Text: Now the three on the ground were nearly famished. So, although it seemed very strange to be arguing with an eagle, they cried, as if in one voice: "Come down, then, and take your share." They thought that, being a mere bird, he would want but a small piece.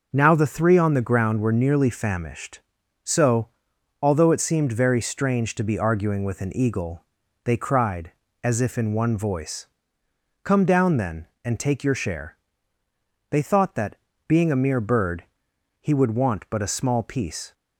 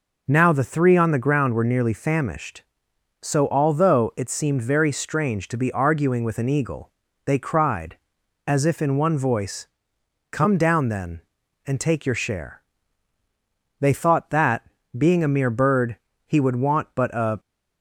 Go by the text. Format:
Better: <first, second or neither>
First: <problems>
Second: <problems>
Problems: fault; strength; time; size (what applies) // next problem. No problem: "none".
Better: first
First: none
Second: stops before "small piece"; at 17.3 s